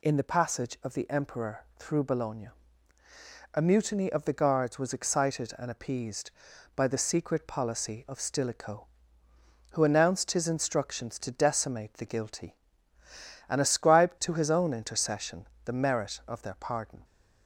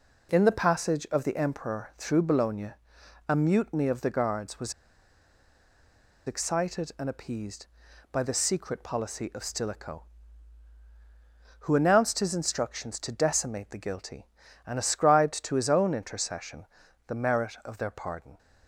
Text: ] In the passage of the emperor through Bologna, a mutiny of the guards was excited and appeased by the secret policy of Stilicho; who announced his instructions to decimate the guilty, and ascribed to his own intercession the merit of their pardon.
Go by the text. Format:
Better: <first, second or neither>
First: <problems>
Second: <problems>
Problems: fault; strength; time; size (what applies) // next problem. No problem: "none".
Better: first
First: pauses between "intercession" and "the"; slight; at 15.4 s; 0.20 s long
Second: pauses between "was" and "excited"; strong; at 4.7 s; 1.5 s long // pauses between "intercession" and "the"; at 16.6 s; 0.44 s long